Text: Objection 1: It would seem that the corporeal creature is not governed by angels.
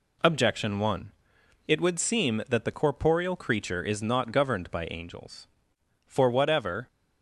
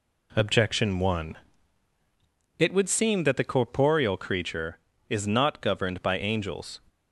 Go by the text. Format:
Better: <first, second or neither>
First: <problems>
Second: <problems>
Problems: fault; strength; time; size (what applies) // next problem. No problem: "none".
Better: second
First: goes on to say "For whatever"; noticeable; from 6.0 s on; 0.82 s long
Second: none